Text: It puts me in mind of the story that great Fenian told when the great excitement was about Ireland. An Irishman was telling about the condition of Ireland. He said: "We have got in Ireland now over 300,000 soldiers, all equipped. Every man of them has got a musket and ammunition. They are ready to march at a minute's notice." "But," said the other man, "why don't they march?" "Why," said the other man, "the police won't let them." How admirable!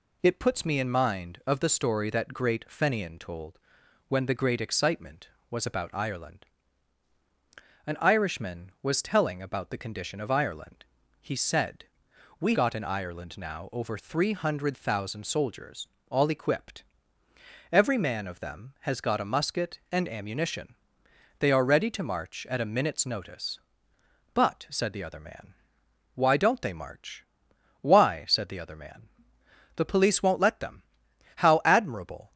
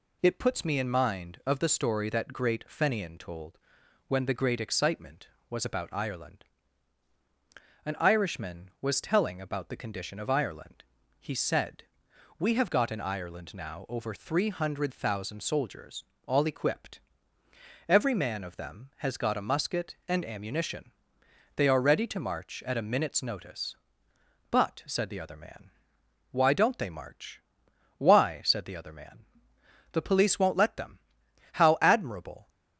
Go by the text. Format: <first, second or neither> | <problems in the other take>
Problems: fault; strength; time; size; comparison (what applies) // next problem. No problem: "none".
second | pauses between "told" and "when"; noticeable; at 3.5 s; 0.48 s long; noticeable in the second // skips "have"; at 12.5 s